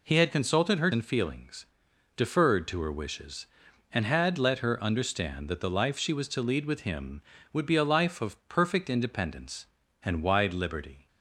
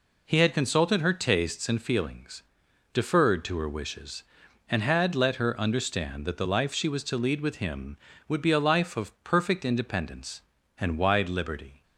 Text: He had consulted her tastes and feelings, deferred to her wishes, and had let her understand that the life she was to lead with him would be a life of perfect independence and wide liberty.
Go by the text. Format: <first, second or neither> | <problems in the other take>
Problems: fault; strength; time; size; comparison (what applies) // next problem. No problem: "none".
second | skips "tastes"; at 0.9 s